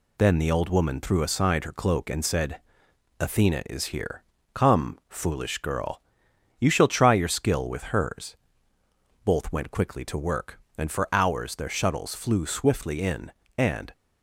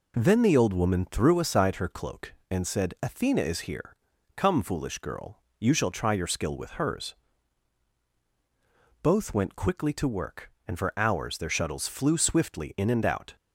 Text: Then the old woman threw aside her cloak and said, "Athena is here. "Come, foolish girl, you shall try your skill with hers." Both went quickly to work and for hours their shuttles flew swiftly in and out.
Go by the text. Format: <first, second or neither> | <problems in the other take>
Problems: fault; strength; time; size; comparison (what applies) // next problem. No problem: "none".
second | stops before "out"; at 13.9 s